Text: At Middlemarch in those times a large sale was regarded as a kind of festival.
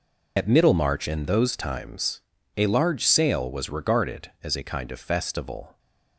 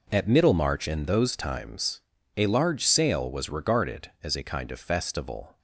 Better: second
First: loses the start of "At"; at 0.3 s; 90 ms // pauses between "times" and "a"; at 2.2 s; 0.38 s long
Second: pauses between "times" and "a"; at 2.0 s; 0.38 s long

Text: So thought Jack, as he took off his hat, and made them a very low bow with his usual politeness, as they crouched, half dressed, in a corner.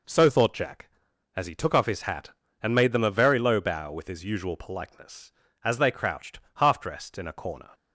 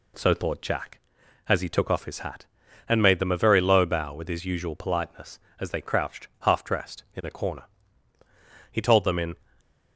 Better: first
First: none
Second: goes on to say "He told them in"; noticeable; from 8.7 s on; 0.64 s long // stays silent after the last word; slight; from 9.3 s on; 0.6 s long

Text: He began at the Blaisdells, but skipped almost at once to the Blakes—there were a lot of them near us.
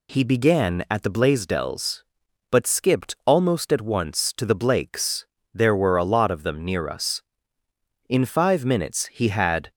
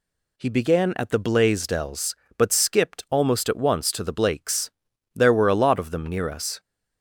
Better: second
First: goes on to say "In five minutes he had"; from 8.0 s on; 1.6 s long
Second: none

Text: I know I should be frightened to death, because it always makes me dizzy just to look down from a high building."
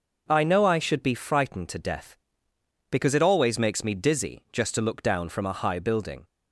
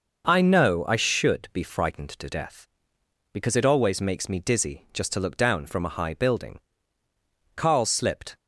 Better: first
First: none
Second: goes on to say "Carl slipped"; noticeable; from 7.5 s on; 0.82 s long

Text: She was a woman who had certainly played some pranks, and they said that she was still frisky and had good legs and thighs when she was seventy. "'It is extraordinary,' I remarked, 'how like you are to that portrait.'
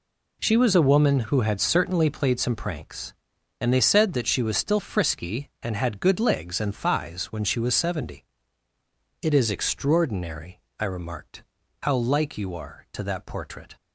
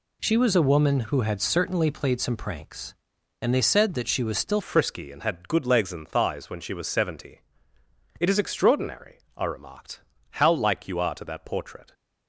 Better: first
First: none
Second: changes voice at "frisky"; from 4.6 s on; 7.3 s long

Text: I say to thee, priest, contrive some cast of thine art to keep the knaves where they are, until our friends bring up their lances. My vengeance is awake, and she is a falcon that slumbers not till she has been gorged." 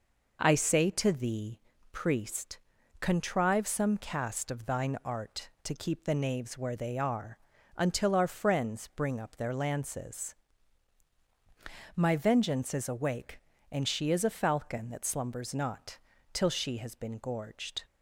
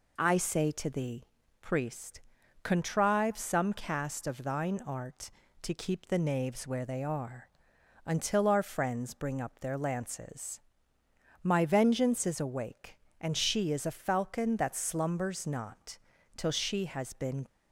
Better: first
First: pauses between "not" and "till"; slight; at 15.9 s; 0.34 s long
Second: pauses between "not" and "till"; at 15.9 s; 0.40 s long // stops before "gorged"; at 17.4 s

